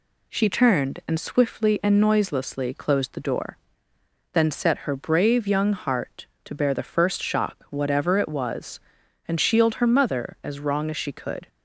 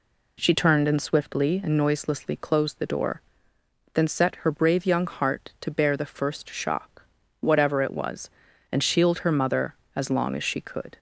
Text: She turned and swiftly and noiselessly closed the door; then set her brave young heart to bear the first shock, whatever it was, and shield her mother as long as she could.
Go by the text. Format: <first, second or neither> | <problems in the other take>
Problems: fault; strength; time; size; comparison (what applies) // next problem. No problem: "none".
second | says "wrong" for "long"; at 10.6 s